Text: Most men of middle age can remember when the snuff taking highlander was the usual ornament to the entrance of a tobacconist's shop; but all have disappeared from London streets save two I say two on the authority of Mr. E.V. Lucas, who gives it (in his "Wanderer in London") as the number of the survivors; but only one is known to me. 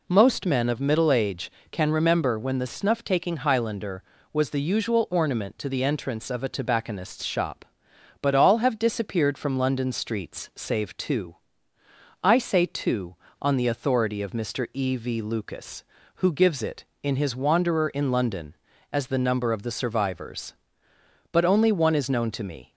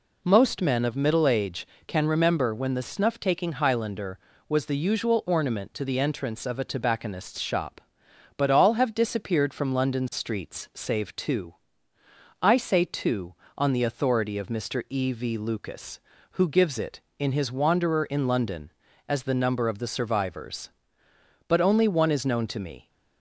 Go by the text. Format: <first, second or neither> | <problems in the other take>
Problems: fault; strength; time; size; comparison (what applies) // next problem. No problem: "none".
neither | pauses between "two" and "I"; noticeable; the same in both